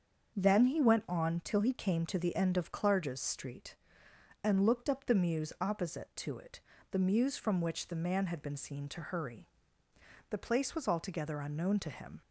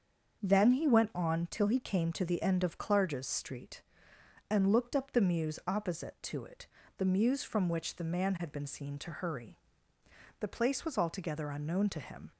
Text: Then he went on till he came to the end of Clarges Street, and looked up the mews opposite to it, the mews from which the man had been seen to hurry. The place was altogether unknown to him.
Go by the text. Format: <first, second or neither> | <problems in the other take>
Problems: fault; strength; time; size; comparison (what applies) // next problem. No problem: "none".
neither | starts louder than the rest; the same in both